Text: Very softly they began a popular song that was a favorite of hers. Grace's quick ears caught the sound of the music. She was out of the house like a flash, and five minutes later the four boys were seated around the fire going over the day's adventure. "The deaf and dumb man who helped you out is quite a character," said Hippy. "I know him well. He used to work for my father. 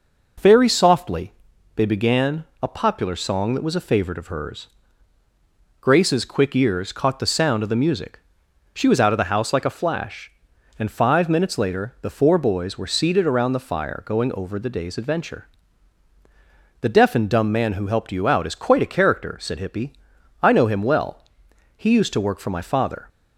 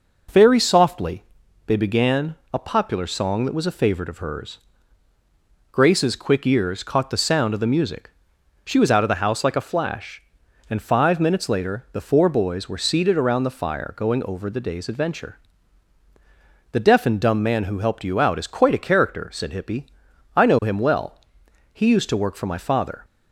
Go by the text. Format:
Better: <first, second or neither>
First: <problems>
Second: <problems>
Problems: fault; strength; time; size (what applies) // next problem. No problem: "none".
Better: neither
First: pauses between "softly" and "they"; at 1.3 s; 0.42 s long // pauses between "began" and "a"; slight; at 2.4 s; 0.18 s long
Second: pauses between "softly" and "they"; at 1.2 s; 0.42 s long // pauses between "began" and "a"; slight; at 2.3 s; 0.18 s long